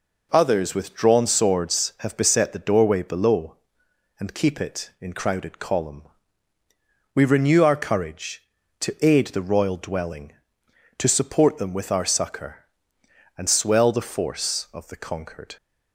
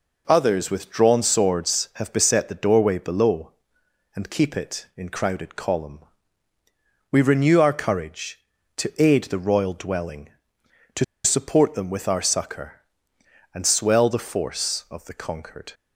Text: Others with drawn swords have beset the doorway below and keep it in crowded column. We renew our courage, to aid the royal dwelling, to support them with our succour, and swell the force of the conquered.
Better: first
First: none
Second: pauses between "to" and "support"; slight; at 11.0 s; 0.21 s long

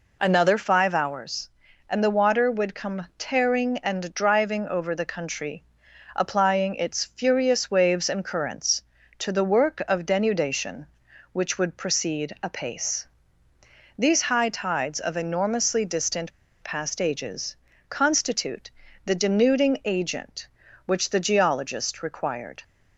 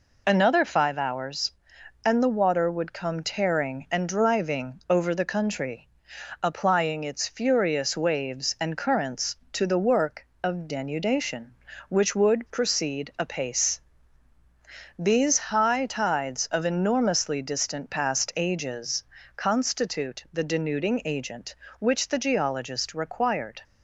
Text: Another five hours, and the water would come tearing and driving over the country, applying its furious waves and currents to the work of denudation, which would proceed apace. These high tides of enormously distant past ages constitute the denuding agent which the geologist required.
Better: second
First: pauses between "distant" and "past"; slight; at 16.3 s; 0.31 s long // pauses between "ages" and "constitute"; slight; at 17.5 s; 0.32 s long // pauses between "constitute" and "the"; slight; at 18.7 s; 0.34 s long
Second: pauses between "ages" and "constitute"; slight; at 19.0 s; 0.32 s long

